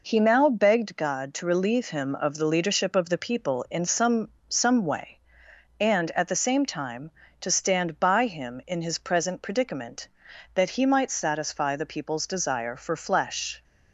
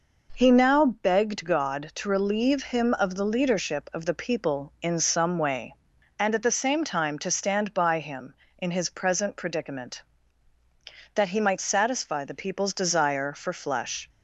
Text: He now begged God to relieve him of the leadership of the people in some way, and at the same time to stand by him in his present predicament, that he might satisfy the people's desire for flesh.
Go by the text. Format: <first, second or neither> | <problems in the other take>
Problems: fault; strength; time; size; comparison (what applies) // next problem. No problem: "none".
second | says "some" twice; at 4.4 s